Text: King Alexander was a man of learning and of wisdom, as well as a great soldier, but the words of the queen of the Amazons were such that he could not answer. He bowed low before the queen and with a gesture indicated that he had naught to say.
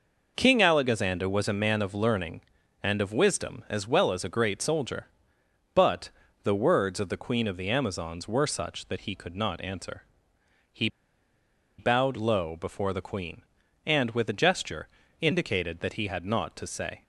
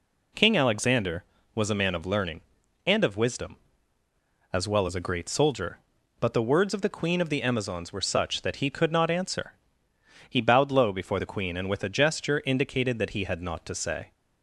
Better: second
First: pauses between "but" and "the"; slight; at 6.0 s; 0.34 s long // pauses between "He" and "bowed"; noticeable; at 10.8 s; 0.89 s long // pauses between "gesture" and "indicated"; slight; at 14.8 s; 0.34 s long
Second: none

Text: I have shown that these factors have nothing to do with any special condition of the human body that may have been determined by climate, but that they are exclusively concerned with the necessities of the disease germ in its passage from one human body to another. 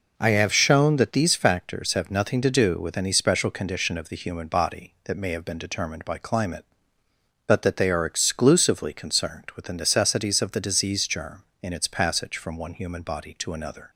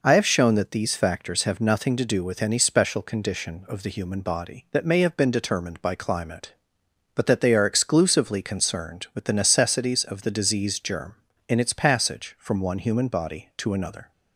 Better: neither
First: none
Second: none

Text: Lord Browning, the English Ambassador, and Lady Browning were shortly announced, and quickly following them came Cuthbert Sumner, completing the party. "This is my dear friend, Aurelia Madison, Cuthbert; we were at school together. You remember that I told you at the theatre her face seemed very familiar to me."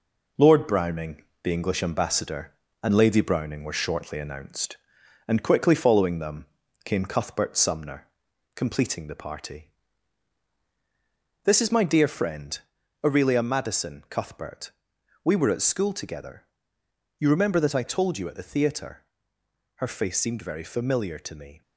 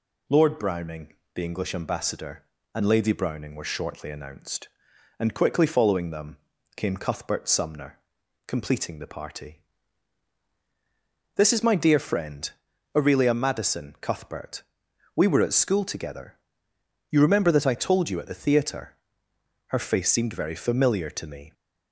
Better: second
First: gets quieter; noticeable; throughout; 4.5 dB // pauses between "them" and "came"; at 6.4 s; 0.40 s long // pauses between "theatre" and "her"; noticeable; at 19.0 s; 0.72 s long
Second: pauses between "them" and "came"; at 6.3 s; 0.40 s long // pauses between "theatre" and "her"; noticeable; at 18.9 s; 0.72 s long

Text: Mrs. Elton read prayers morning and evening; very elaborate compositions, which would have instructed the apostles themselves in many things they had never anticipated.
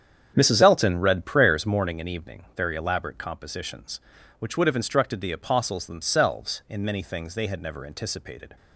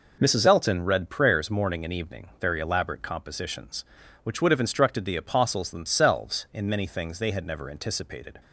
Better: second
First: starts louder than the rest; strong; until 2.0 s; 8 dB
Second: none

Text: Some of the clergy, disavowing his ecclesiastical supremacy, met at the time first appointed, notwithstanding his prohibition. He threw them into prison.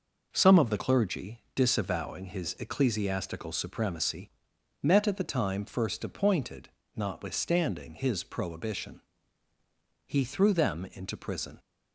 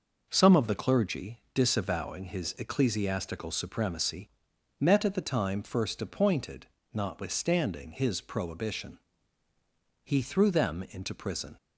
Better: neither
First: none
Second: none

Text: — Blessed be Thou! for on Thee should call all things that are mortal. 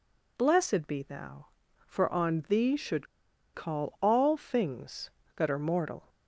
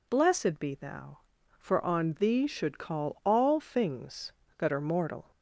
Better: second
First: pauses between "should" and "call"; noticeable; at 3.0 s; 0.47 s long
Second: none

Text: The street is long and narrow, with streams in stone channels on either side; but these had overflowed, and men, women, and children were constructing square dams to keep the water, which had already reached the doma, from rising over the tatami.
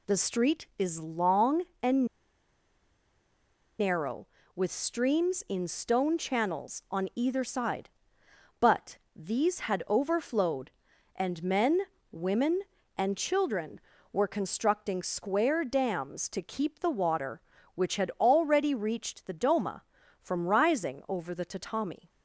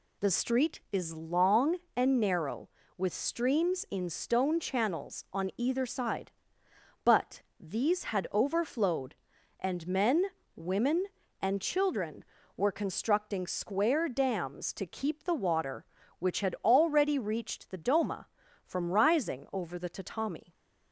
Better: second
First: pauses between "and" and "narrow"; strong; at 2.0 s; 1.7 s long // pauses between "but" and "these"; slight; at 8.9 s; 0.18 s long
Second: pauses between "but" and "these"; slight; at 7.4 s; 0.18 s long

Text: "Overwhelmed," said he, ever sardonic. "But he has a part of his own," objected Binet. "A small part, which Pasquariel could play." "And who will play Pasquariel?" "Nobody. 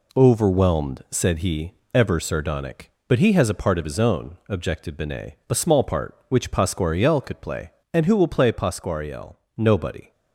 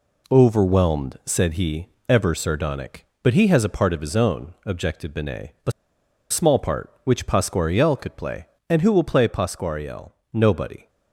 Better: first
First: none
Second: pauses between "A" and "small"; noticeable; at 5.7 s; 0.59 s long

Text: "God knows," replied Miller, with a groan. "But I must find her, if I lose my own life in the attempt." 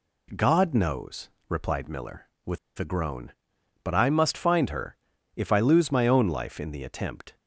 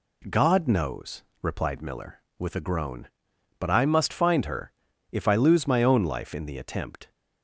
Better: second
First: pauses between "with" and "a"; slight; at 2.5 s; 0.20 s long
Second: none

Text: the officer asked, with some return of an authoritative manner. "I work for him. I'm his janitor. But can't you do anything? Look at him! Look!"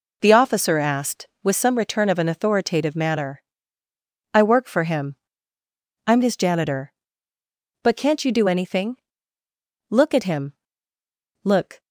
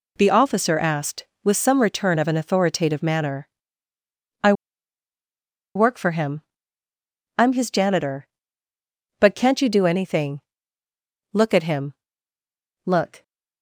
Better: first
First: none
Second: pauses between "I" and "work"; at 4.5 s; 1.2 s long

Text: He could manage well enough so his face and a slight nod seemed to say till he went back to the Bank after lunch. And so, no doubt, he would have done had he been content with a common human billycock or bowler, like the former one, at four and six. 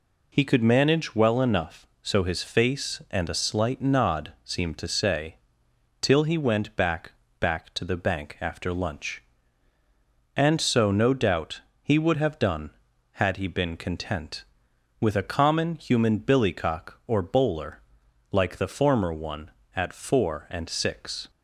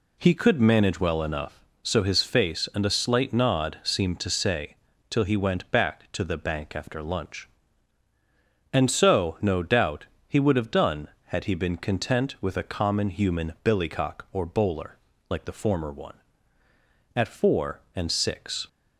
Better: second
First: pauses between "say" and "till"; noticeable; at 5.3 s; 0.66 s long // says "back" twice; at 7.3 s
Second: pauses between "say" and "till"; slight; at 4.7 s; 0.36 s long

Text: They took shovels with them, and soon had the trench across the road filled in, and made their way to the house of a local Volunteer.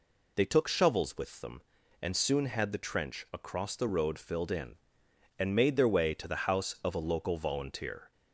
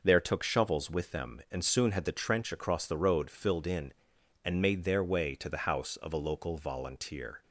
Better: first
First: none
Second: says "There" for "They"; at 0.0 s

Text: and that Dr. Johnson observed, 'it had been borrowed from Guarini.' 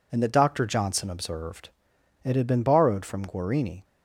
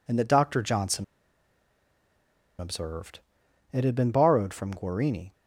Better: first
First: none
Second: pauses between "Johnson" and "observed"; strong; at 1.0 s; 1.5 s long

